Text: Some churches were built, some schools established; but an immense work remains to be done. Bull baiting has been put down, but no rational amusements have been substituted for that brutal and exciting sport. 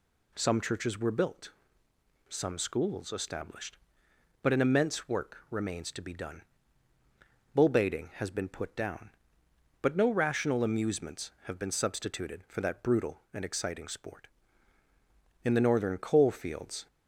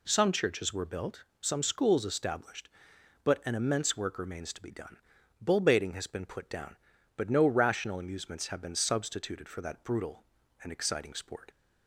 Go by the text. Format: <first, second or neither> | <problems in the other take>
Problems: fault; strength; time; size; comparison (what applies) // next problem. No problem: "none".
second | goes on to say "In the northern coal fields"; from 15.4 s on; 1.4 s long